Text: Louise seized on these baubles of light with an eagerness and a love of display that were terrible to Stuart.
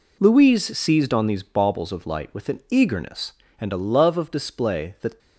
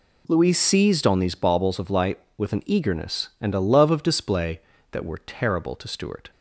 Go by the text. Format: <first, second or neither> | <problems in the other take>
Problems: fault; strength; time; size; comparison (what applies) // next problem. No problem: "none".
second | stops before "were terrible to Stuart"; at 5.1 s